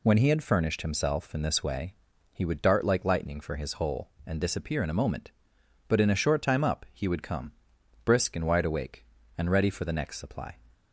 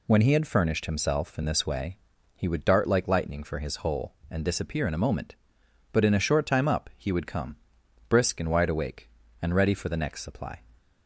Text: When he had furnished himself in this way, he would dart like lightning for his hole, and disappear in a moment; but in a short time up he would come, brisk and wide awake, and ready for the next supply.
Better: neither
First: none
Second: none

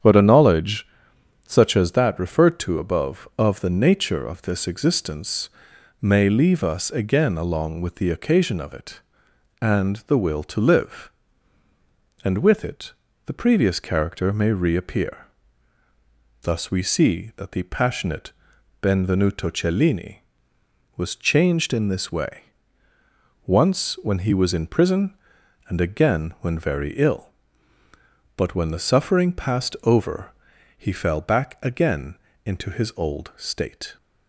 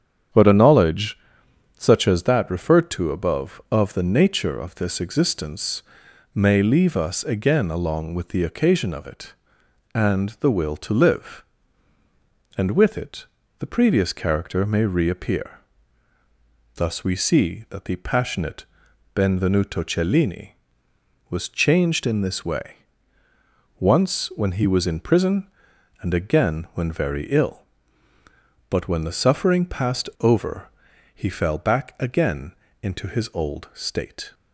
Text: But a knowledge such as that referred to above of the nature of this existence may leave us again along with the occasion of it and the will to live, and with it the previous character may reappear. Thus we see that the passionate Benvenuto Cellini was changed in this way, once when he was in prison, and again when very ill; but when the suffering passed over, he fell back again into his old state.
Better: neither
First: starts louder than the rest; strong; until 1.6 s; 8.5 dB // pauses between "knowledge" and "such"; noticeable; at 0.8 s; 0.58 s long // pauses between "existence" and "may"; noticeable; at 5.4 s; 0.52 s long // pauses between "it" and "the"; slight; at 12.9 s; 0.34 s long // pauses between "passionate" and "Benvenuto"; noticeable; at 18.3 s; 0.50 s long // pauses between "again" and "into"; slight; at 32.1 s; 0.30 s long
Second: starts louder than the rest; strong; until 1.9 s; 8.5 dB // pauses between "knowledge" and "such"; noticeable; at 1.1 s; 0.58 s long // pauses between "existence" and "may"; noticeable; at 5.8 s; 0.52 s long // pauses between "it" and "the"; slight; at 13.2 s; 0.34 s long // pauses between "passionate" and "Benvenuto"; noticeable; at 18.6 s; 0.50 s long // pauses between "again" and "into"; slight; at 32.5 s; 0.30 s long

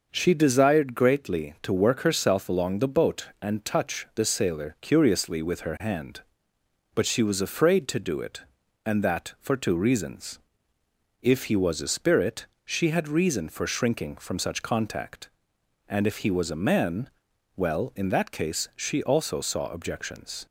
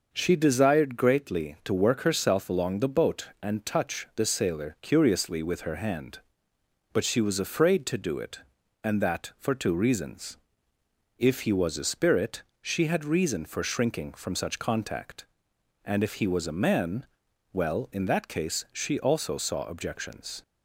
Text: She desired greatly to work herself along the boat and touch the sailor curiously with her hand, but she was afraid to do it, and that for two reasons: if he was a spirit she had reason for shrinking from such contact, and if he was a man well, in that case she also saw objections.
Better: neither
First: pauses between "spirit" and "she"; slight; at 12.4 s; 0.20 s long // pauses between "man" and "well"; noticeable; at 17.0 s; 0.46 s long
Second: pauses between "spirit" and "she"; slight; at 12.4 s; 0.20 s long // pauses between "man" and "well"; noticeable; at 17.0 s; 0.46 s long

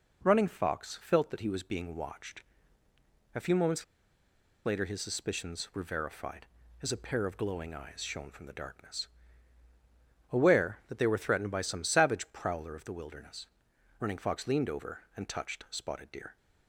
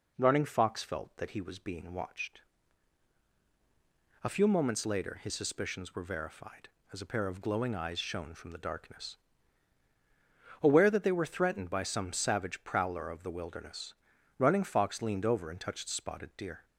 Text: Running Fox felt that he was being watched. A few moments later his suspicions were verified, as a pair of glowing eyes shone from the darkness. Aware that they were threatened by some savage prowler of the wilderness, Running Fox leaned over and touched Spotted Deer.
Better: second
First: pauses between "moments" and "later"; noticeable; at 3.8 s; 0.81 s long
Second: none

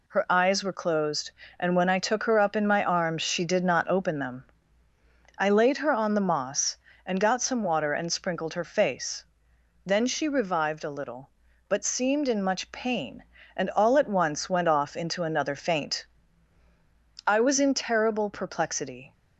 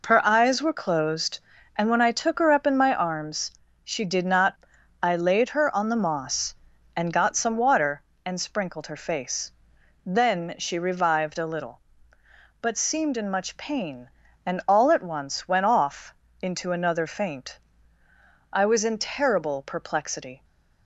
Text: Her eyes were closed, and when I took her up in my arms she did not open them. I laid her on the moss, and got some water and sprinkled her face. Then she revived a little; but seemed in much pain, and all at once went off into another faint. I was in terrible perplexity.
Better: first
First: none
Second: pauses between "arms" and "she"; slight; at 3.5 s; 0.32 s long // skips "open them"; at 4.7 s // pauses between "off" and "into"; slight; at 16.1 s; 0.26 s long

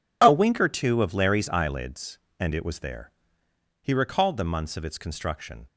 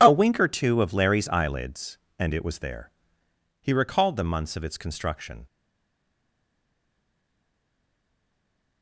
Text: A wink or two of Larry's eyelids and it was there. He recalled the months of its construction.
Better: first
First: none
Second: stays silent after the last word; strong; from 5.4 s on; 3.4 s long

